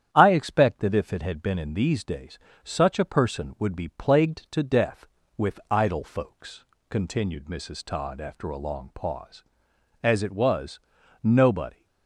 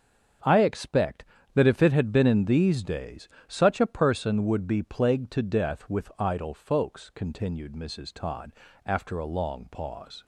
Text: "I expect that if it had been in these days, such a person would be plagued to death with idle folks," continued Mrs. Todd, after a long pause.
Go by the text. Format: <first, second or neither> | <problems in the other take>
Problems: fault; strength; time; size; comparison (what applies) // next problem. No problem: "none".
second | starts louder than the rest; strong; until 1.1 s; 9.5 dB; strong in the second // goes on to say "As it was nobody"; strong; from 10.0 s on; 1.8 s long